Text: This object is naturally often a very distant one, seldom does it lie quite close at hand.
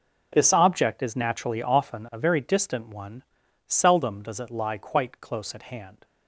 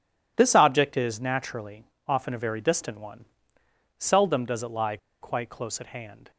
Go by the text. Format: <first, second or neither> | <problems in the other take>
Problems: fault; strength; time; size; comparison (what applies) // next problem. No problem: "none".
first | pauses between "naturally" and "often"; slight; at 1.8 s; 0.24 s long // pauses between "lie" and "quite"; slight; at 4.9 s; 0.24 s long